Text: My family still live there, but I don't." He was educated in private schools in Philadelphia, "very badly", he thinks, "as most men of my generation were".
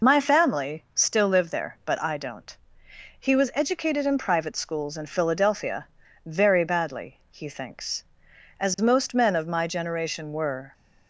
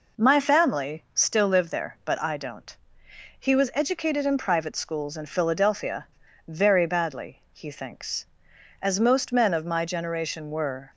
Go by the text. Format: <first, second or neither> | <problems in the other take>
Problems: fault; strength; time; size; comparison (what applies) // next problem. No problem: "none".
second | loses the start of "My"; at 0.0 s; 50 ms